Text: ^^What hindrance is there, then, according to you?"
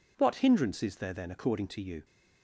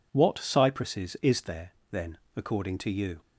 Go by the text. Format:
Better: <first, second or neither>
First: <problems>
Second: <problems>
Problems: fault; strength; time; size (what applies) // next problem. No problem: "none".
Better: first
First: none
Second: says "cypresses" for "hindrance"; at 0.3 s